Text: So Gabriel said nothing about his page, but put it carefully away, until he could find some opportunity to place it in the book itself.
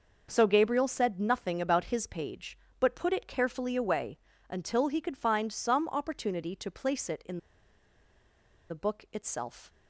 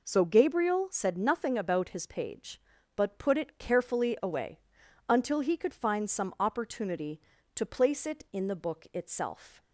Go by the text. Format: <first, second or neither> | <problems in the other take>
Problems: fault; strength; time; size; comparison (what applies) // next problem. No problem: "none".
second | pauses between "in" and "the"; strong; at 7.3 s; 1.3 s long